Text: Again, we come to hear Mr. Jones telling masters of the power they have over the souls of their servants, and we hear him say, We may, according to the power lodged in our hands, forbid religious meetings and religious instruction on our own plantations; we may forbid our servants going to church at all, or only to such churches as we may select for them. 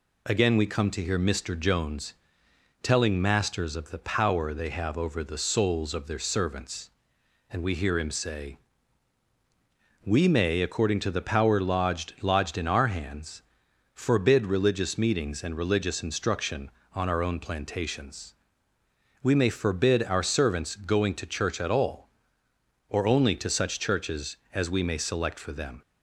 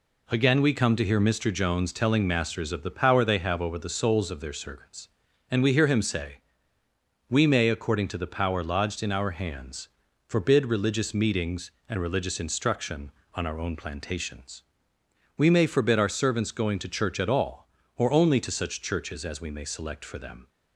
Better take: second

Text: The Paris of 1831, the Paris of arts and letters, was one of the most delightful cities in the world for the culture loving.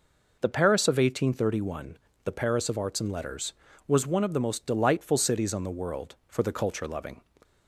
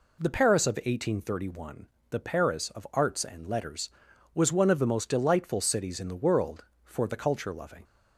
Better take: second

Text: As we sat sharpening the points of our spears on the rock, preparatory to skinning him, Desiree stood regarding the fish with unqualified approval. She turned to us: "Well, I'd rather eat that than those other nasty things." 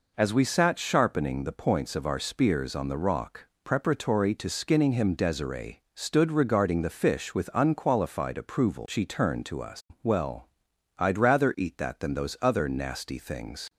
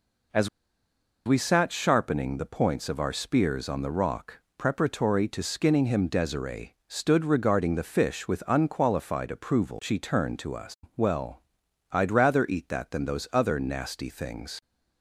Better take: first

